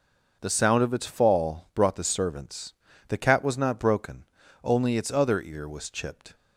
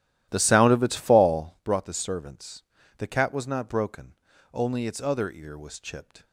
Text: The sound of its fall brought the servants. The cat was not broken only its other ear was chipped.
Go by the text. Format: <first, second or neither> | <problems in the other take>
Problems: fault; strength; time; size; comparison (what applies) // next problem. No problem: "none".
first | starts louder than the rest; strong; until 1.6 s; 13 dB // pauses between "broken" and "only"; at 4.1 s; 0.38 s long; also in the first